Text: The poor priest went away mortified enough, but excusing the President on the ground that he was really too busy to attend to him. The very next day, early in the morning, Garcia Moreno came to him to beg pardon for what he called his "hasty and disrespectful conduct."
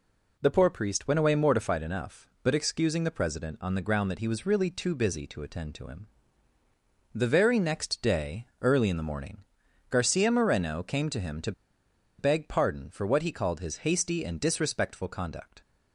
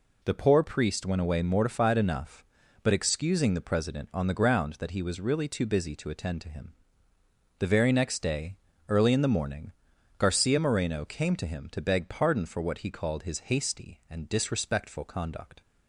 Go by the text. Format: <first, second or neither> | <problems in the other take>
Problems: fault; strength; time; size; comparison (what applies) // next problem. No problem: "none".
second | pauses between "to" and "beg"; noticeable; at 11.5 s; 0.67 s long